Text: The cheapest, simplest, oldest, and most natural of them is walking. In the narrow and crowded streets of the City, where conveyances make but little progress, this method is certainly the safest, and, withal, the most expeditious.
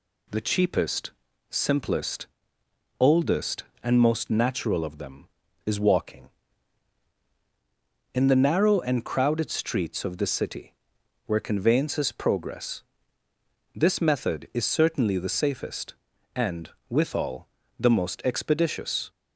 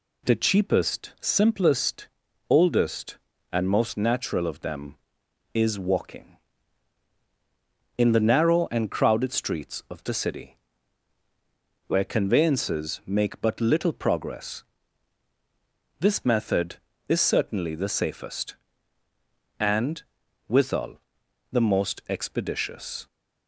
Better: second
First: skips "make but little"; at 12.1 s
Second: none

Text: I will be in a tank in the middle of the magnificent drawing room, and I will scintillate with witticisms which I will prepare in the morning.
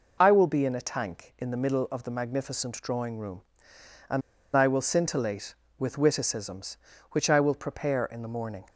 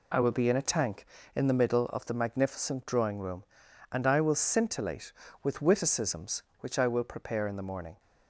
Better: second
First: pauses between "and" and "I"; slight; at 4.2 s; 0.35 s long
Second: none

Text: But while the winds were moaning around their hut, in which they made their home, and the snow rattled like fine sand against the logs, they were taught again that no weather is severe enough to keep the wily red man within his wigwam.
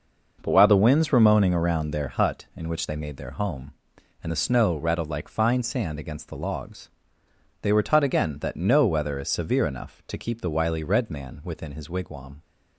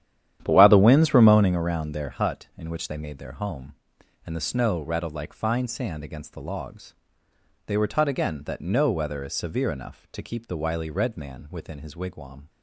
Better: first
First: none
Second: starts louder than the rest; strong; until 1.6 s; 10.5 dB

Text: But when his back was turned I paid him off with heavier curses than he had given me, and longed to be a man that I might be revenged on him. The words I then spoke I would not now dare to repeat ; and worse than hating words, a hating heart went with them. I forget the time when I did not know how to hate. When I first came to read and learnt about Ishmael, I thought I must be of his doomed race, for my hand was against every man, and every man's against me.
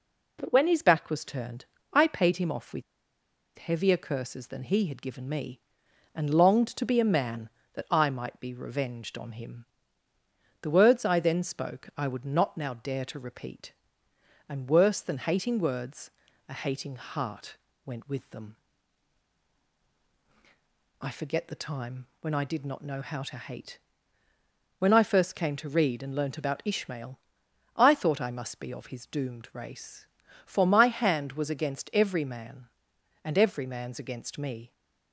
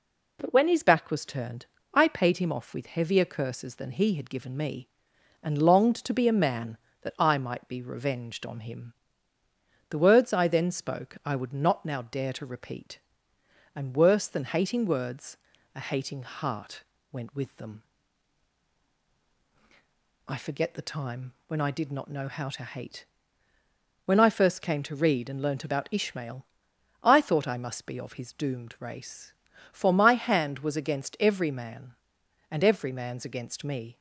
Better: second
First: pauses between "turned" and "I"; slight; at 1.6 s; 0.26 s long // pauses between "with" and "heavier"; noticeable; at 2.8 s; 0.75 s long // pauses between "heart" and "went"; slight; at 17.5 s; 0.26 s long // pauses between "time" and "when"; slight; at 22.0 s; 0.16 s long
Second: pauses between "turned" and "I"; slight; at 1.6 s; 0.26 s long // pauses between "heart" and "went"; slight; at 16.8 s; 0.26 s long // pauses between "time" and "when"; slight; at 21.3 s; 0.16 s long

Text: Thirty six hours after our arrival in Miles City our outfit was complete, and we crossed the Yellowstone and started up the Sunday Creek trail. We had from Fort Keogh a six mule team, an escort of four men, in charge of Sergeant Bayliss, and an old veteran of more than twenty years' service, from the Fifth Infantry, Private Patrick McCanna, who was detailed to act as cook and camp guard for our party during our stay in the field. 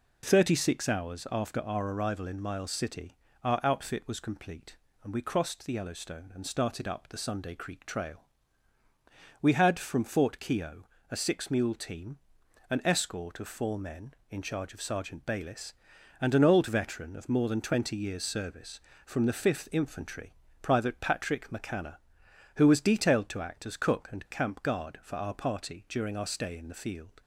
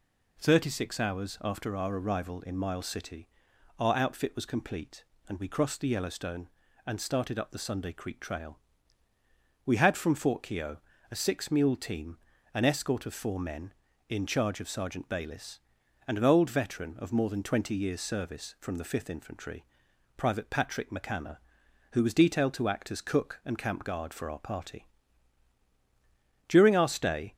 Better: first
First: pauses between "City" and "our"; slight; at 3.1 s; 0.30 s long // pauses between "Keogh" and "a"; slight; at 10.8 s; 0.24 s long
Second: pauses between "City" and "our"; noticeable; at 3.2 s; 0.50 s long // pauses between "Keogh" and "a"; slight; at 10.7 s; 0.34 s long // pauses between "party" and "during"; strong; at 24.8 s; 1.6 s long // stops before "in the field"; at 27.3 s

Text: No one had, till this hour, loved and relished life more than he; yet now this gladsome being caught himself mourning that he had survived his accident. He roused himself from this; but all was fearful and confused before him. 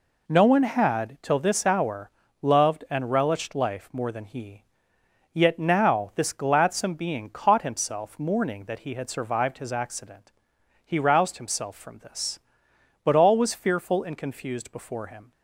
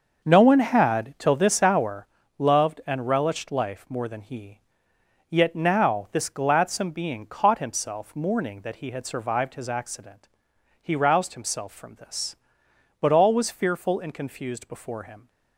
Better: first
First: none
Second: starts louder than the rest; until 2.1 s; 6 dB

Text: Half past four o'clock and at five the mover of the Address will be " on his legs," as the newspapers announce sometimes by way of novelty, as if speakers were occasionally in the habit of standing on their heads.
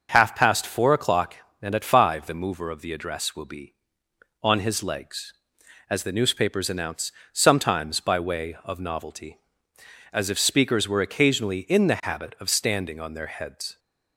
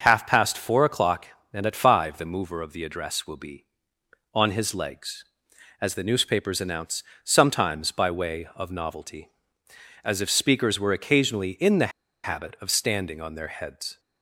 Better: first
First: starts louder than the rest; until 1.1 s; 6.5 dB // pauses between "announce" and "sometimes"; slight; at 7.1 s; 0.20 s long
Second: starts louder than the rest; until 1.0 s; 6.5 dB // pauses between "announce" and "sometimes"; slight; at 7.0 s; 0.20 s long // pauses between "the" and "habit"; slight; at 11.9 s; 0.34 s long

